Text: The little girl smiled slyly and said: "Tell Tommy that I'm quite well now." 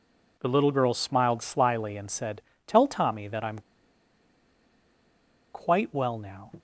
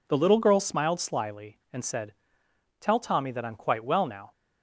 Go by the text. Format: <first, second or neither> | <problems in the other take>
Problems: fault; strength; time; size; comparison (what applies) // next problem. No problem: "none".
second | pauses between "I'm" and "quite"; strong; at 3.5 s; 1.9 s long